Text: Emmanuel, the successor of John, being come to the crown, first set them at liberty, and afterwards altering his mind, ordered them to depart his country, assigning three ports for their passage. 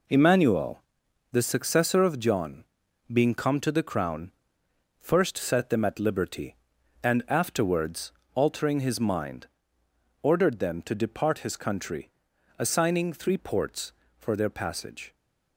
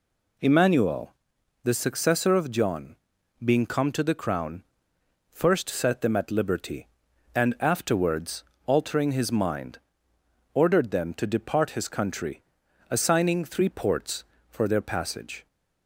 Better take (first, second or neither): second